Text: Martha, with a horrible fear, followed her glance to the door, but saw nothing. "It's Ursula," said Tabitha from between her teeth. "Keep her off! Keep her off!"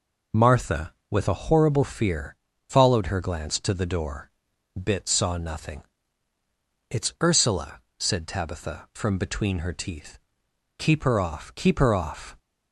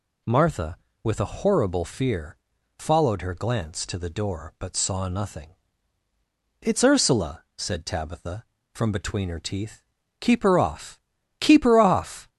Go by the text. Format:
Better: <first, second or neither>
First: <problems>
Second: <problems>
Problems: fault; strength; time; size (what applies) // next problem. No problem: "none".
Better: second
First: says "bit" for "but"; at 4.8 s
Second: none